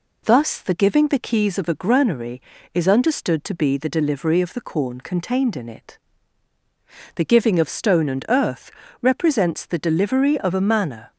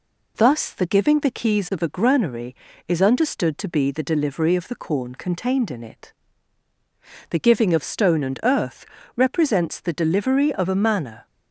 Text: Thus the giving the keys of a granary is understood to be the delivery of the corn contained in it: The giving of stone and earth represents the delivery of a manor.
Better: neither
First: pauses between "earth" and "represents"; slight; at 8.7 s; 0.30 s long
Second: pauses between "earth" and "represents"; slight; at 8.8 s; 0.30 s long

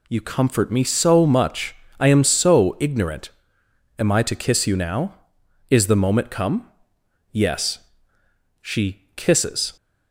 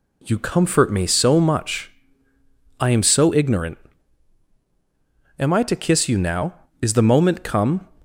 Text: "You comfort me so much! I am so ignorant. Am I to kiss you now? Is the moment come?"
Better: second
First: goes on to say "Yes She kisses"; strong; from 7.3 s on; 2.4 s long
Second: none

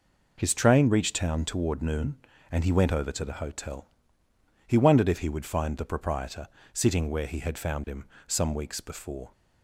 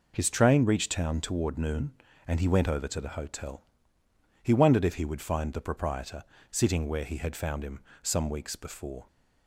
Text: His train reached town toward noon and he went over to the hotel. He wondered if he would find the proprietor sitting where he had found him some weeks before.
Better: neither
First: pauses between "proprietor" and "sitting"; slight; at 6.4 s; 0.26 s long // pauses between "him" and "some"; slight; at 8.0 s; 0.20 s long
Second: pauses between "proprietor" and "sitting"; slight; at 6.2 s; 0.29 s long // pauses between "him" and "some"; slight; at 7.8 s; 0.20 s long

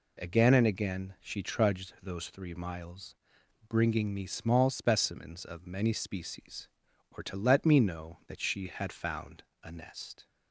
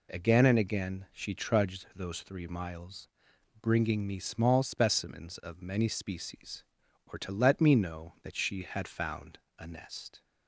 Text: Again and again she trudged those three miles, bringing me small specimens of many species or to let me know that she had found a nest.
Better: neither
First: pauses between "found" and "a"; slight; at 9.4 s; 0.20 s long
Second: pauses between "found" and "a"; slight; at 9.3 s; 0.20 s long

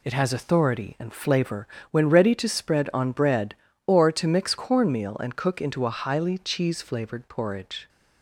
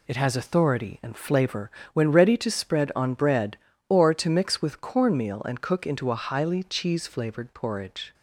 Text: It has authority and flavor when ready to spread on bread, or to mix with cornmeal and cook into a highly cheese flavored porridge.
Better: second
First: pauses between "flavor" and "when"; slight; at 1.6 s; 0.24 s long // skips "with"; at 4.5 s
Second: pauses between "flavor" and "when"; slight; at 1.7 s; 0.23 s long

